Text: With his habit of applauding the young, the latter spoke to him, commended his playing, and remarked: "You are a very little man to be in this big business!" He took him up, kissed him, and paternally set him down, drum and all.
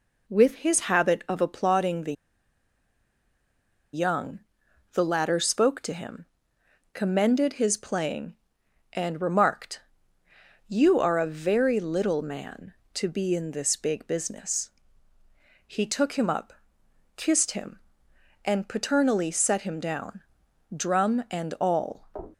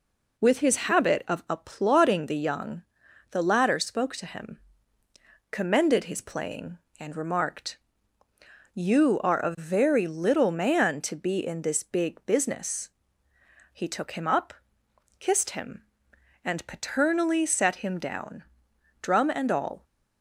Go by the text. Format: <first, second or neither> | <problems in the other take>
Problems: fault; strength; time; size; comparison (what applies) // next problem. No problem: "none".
second | pauses between "the" and "young"; strong; at 2.1 s; 1.7 s long